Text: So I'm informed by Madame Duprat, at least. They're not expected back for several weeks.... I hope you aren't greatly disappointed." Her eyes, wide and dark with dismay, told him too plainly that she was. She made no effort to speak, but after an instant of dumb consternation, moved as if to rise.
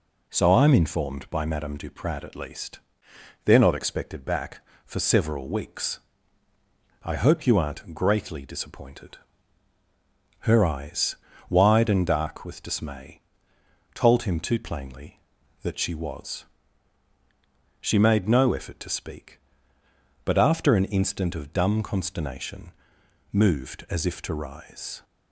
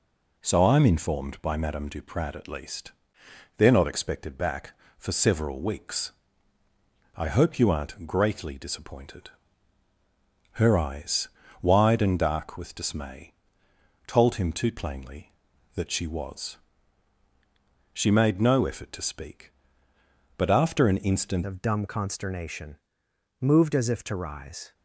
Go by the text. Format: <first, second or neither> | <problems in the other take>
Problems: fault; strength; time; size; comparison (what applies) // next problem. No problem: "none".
first | changes voice at "of"; from 21.4 s on; 3.3 s long